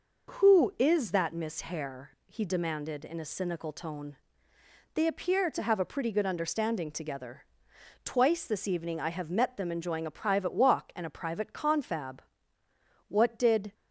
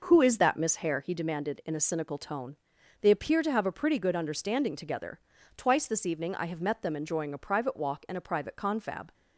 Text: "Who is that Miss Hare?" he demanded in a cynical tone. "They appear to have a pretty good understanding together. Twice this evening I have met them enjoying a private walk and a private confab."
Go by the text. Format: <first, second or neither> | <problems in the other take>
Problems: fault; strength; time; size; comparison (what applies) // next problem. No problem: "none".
second | goes on to say "What did"; noticeable; from 13.0 s on; 0.66 s long